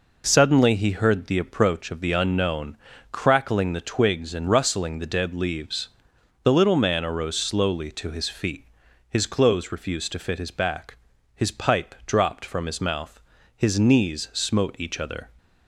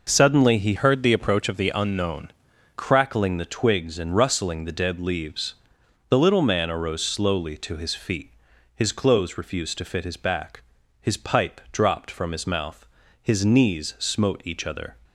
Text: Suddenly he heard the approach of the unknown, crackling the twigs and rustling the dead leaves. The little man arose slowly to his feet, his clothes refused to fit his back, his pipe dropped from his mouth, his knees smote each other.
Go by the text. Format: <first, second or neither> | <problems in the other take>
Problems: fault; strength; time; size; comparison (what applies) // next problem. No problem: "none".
first | changes voice from "heard" to "unknown"; from 0.7 to 2.3 s; 1.6 s long